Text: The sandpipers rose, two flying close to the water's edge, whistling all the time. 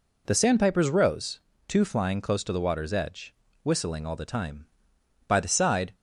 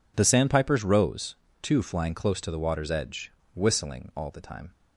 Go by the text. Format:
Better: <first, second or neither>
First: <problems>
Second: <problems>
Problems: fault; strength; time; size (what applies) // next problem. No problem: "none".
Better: second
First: goes on to say "By the side"; noticeable; from 5.2 s on; 0.66 s long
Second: none